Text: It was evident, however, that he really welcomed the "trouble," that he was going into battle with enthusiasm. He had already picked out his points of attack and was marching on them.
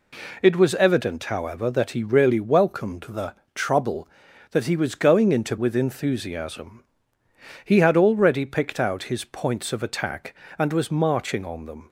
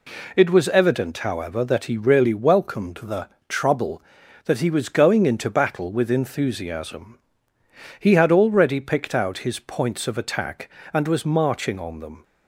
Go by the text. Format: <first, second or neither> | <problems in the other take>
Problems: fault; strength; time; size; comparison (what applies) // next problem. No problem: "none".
second | pauses between "the" and "trouble"; slight; at 3.3 s; 0.22 s long; slight in the second // skips "battle"; at 5.5 s